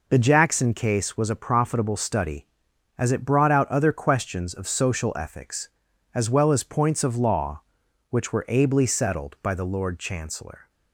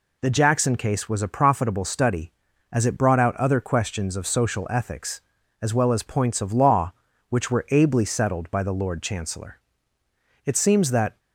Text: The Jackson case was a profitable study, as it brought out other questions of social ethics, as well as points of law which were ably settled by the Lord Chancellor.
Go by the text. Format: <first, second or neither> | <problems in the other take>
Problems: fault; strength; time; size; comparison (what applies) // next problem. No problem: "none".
first | goes on to say "It seems that"; noticeable; from 10.4 s on; 0.72 s long